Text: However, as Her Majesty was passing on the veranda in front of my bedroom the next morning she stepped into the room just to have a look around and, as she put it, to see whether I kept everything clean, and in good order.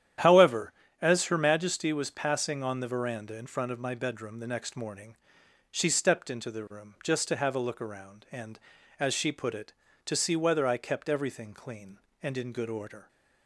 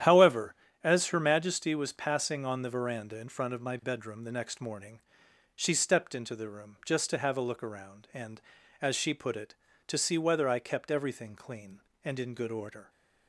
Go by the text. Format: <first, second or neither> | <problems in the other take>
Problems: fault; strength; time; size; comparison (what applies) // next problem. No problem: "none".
neither | starts louder than the rest; strong; the same in both // pauses between "morning" and "she"; noticeable; the same in both